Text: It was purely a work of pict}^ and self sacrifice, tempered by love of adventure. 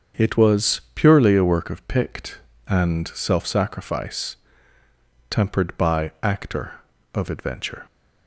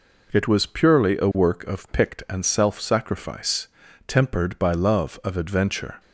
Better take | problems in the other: second | starts louder than the rest; strong; until 1.3 s; 7.5 dB // says "actor" for "love"; at 6.2 s

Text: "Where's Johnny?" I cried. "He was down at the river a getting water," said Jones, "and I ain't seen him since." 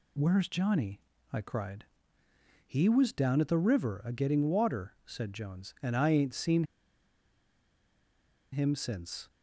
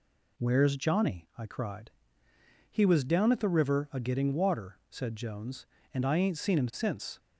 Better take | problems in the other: second | pauses between "seen" and "him"; strong; at 6.6 s; 1.8 s long

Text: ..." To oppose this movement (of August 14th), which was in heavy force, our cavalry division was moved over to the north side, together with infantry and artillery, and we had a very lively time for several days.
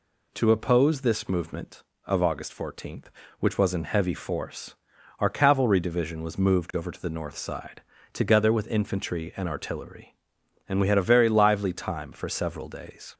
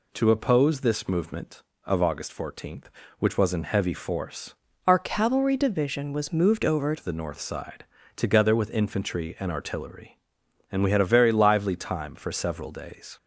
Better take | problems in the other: first | changes voice from "our" to "over"; from 4.8 to 6.9 s; 2.1 s long

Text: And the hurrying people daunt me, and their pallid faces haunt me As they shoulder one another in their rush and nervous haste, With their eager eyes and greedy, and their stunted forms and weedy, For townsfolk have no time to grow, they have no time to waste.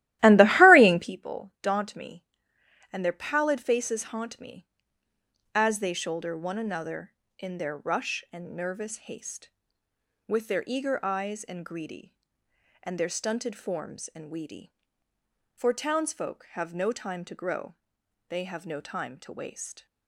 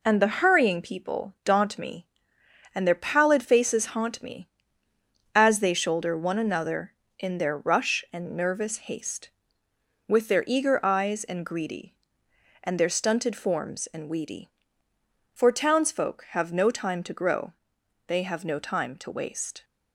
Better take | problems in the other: second | starts louder than the rest; strong; until 1.2 s; 15.5 dB

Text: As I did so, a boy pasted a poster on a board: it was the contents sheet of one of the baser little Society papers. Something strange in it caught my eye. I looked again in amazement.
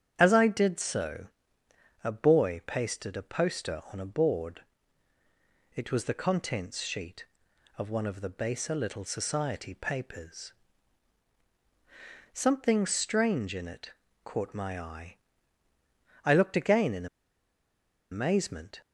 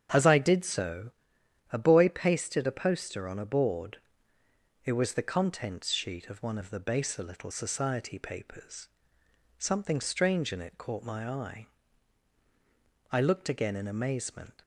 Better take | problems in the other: second | starts louder than the rest; strong; until 1.1 s; 8.5 dB; strong in the second // pauses between "it" and "caught"; slight; at 13.9 s; 0.32 s long // pauses between "in" and "amazement"; at 17.0 s; 1.0 s long

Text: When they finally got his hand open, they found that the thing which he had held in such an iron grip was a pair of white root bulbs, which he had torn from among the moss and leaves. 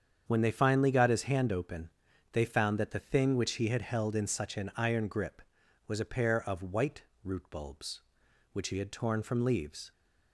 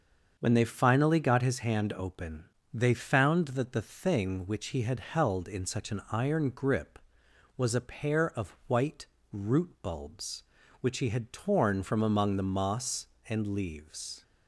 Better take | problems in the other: second | starts louder than the rest; strong; until 1.2 s; 7.5 dB; also in the second // pauses between "white" and "root"; slight; at 7.0 s; 0.20 s long; slight in the second // skips "among the moss and"; at 9.4 s

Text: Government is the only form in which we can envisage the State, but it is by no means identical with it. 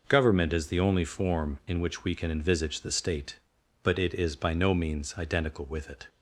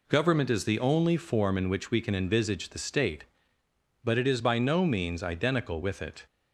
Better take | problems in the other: neither | none

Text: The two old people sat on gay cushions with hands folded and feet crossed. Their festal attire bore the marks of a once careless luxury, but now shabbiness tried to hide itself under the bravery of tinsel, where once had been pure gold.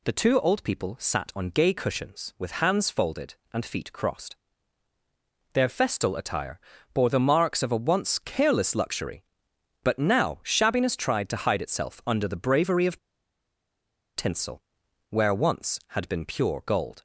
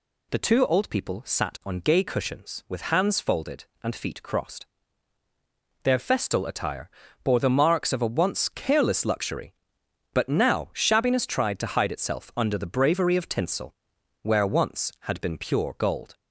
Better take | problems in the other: second | pauses between "attire" and "bore"; slight; at 6.5 s; 0.34 s long; slight in the second // pauses between "of" and "tinsel"; at 12.9 s; 1.1 s long

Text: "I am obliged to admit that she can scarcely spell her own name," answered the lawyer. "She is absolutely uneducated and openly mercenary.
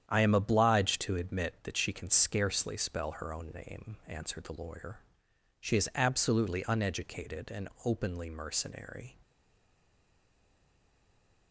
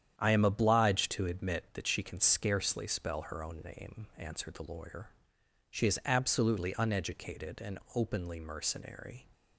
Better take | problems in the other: second | starts louder than the rest; strong; until 1.1 s; 9.5 dB; strong in the second // pauses between "and" and "openly"; slight; at 7.7 s; 0.16 s long; slight in the second // stays silent after the last word; from 9.2 s on; 2.3 s long

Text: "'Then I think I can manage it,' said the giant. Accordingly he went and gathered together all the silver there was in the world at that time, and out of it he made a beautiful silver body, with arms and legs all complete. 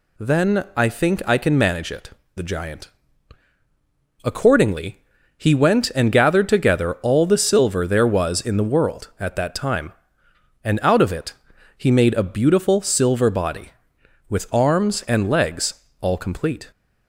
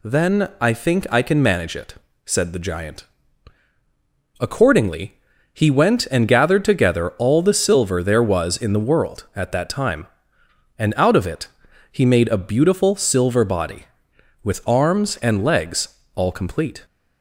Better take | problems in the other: second | skips "said"; at 2.2 s // pauses between "Accordingly" and "he"; at 4.9 s; 0.38 s long; also in the second // pauses between "it" and "he"; at 11.3 s; 0.44 s long; also in the second // pauses between "legs" and "all"; slight; at 15.7 s; 0.26 s long; slight in the second

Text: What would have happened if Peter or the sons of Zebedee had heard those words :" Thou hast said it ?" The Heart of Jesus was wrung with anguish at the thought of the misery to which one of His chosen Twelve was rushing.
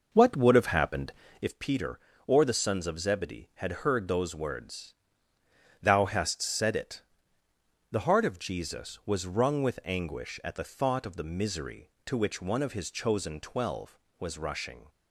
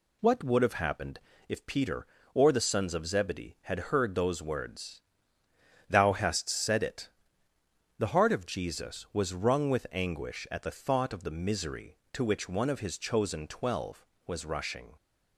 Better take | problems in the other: second | starts louder than the rest; noticeable; until 1.5 s; 6 dB // pauses between "happened" and "if"; slight; at 1.1 s; 0.28 s long; slight in the second

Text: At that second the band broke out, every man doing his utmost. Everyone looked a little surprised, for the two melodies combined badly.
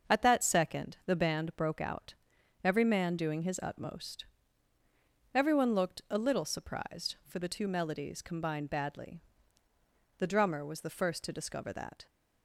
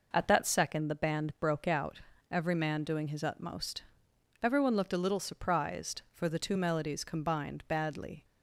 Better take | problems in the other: second | starts louder than the rest; until 1.1 s; 6.5 dB // goes on to say "The drummer was the first to discover that"; strong; from 10.1 s on; 1.8 s long

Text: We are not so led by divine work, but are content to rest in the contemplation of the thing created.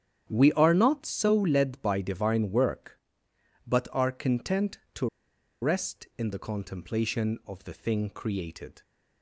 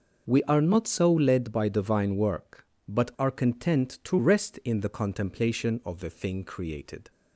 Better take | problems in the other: second | starts louder than the rest; strong; until 1.3 s; 9.5 dB // pauses between "to" and "rest"; noticeable; at 5.0 s; 0.55 s long

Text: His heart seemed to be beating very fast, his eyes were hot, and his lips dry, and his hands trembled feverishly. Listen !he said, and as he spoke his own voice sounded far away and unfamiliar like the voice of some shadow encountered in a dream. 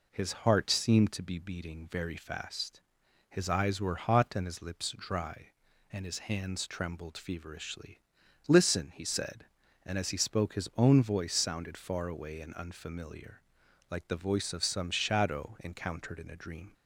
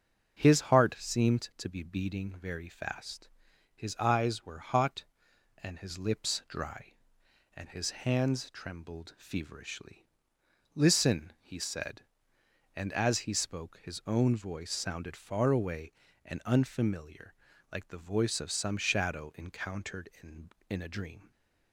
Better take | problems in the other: first | starts louder than the rest; until 1.4 s; 6.5 dB // pauses between "unfamiliar" and "like"; at 17.3 s; 0.40 s long; noticeable in the first // says "in" twice; at 20.6 s

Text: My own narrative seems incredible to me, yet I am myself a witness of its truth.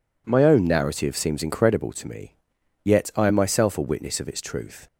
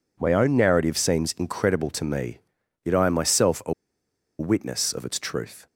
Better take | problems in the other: first | pauses between "a" and "witness"; noticeable; at 3.7 s; 0.66 s long

